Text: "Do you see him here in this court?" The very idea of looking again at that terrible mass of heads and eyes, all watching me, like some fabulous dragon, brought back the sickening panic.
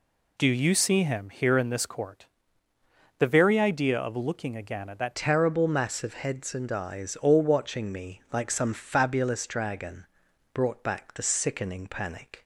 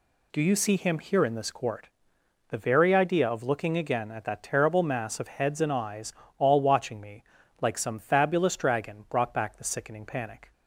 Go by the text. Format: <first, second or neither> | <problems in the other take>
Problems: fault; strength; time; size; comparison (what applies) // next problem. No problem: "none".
second | changes voice at "terrible"; from 5.1 s on; 7.3 s long